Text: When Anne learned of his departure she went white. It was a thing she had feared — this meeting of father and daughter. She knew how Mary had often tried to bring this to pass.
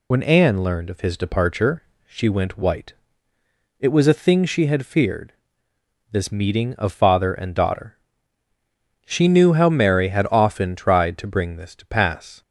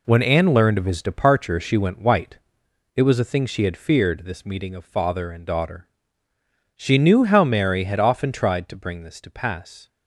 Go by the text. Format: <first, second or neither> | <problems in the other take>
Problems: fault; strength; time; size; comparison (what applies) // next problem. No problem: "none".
second | loses the start of "When"; at 0.1 s; 70 ms // pauses between "departure" and "she"; slight; at 1.8 s; 0.24 s long